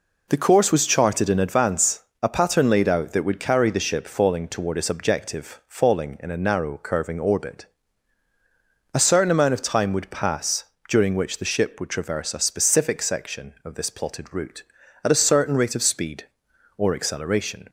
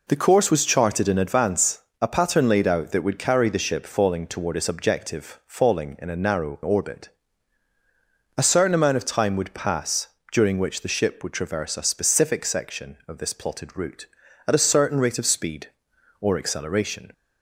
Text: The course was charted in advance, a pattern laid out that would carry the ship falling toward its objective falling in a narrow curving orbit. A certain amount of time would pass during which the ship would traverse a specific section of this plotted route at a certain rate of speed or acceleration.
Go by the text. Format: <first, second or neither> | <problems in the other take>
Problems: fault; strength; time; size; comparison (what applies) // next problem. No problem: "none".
first | skips "curving"; at 6.6 s // pauses between "pass" and "during"; slight; at 10.0 s; 0.24 s long; slight in the first